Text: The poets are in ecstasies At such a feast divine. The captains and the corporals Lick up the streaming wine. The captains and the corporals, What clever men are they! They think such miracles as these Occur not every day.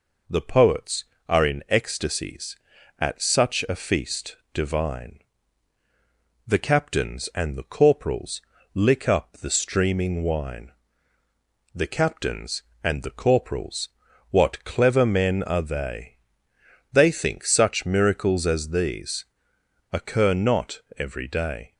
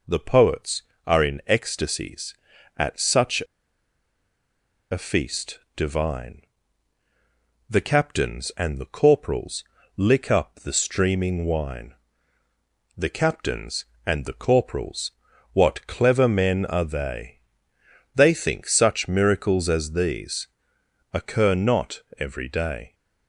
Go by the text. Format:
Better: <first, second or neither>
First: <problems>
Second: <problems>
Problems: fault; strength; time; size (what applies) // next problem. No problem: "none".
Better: first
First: pauses between "feast" and "divine"; slight; at 4.3 s; 0.18 s long // pauses between "corporals" and "Lick"; slight; at 8.4 s; 0.32 s long // pauses between "these" and "Occur"; noticeable; at 19.2 s; 0.69 s long // pauses between "not" and "every"; slight; at 20.8 s; 0.16 s long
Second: pauses between "such" and "a"; strong; at 3.4 s; 1.4 s long // pauses between "feast" and "divine"; slight; at 5.5 s; 0.18 s long // pauses between "corporals" and "Lick"; slight; at 9.6 s; 0.32 s long // pauses between "these" and "Occur"; noticeable; at 20.4 s; 0.68 s long // pauses between "not" and "every"; slight; at 22.0 s; 0.16 s long